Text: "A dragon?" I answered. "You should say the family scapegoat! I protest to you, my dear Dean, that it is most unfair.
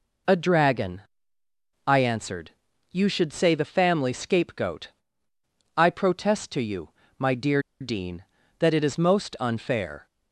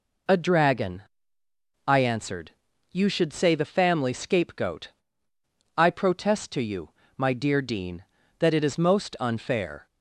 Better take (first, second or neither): second